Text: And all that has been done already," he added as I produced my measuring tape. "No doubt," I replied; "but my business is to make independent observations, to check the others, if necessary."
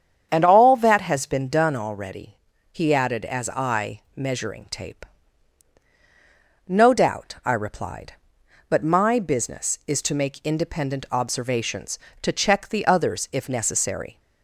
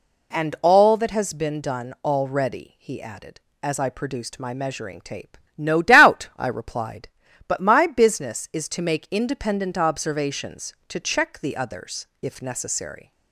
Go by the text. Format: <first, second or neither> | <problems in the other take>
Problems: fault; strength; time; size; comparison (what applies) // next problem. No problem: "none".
second | starts louder than the rest; strong; until 1.3 s; 8 dB // skips "produced my"; at 4.0 s